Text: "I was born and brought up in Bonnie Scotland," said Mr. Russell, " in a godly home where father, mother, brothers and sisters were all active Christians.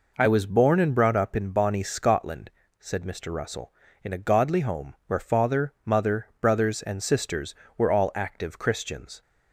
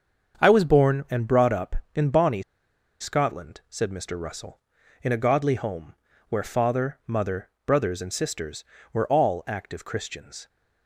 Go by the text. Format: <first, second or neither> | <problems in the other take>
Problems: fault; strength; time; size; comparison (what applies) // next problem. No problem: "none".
first | starts louder than the rest; until 1.4 s; 7 dB // pauses between "Bonnie" and "Scotland"; noticeable; at 2.4 s; 0.58 s long // pauses between "home" and "where"; slight; at 5.9 s; 0.34 s long